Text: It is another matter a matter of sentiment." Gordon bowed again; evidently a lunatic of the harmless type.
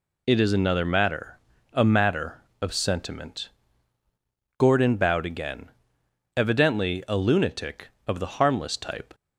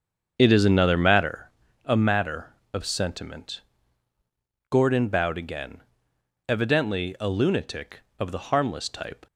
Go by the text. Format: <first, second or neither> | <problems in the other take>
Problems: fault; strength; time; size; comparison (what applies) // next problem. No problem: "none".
first | starts louder than the rest; until 1.5 s; 7 dB // pauses between "matter" and "a"; slight; at 1.5 s; 0.34 s long; slight in the first